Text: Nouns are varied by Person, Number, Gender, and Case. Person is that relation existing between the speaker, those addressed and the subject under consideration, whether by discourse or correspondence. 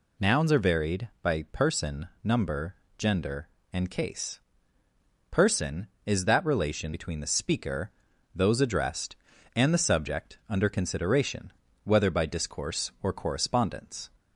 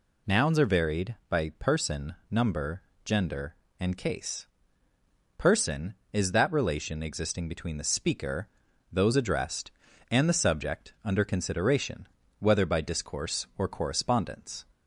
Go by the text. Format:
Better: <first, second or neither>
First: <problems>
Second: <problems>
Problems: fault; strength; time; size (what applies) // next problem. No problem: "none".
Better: second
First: skips "existing"; at 6.9 s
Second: none